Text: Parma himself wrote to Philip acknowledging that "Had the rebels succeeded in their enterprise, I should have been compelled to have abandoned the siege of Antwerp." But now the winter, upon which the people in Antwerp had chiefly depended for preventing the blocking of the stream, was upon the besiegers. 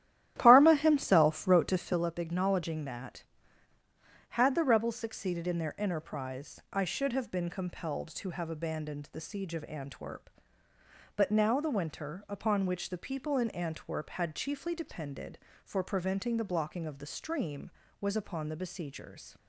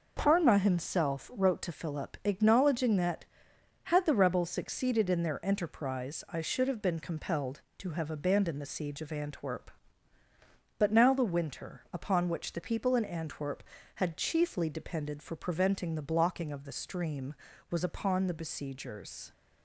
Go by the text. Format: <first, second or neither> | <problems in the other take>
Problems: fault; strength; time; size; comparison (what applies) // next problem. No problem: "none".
second | starts louder than the rest; strong; until 2.1 s; 12.5 dB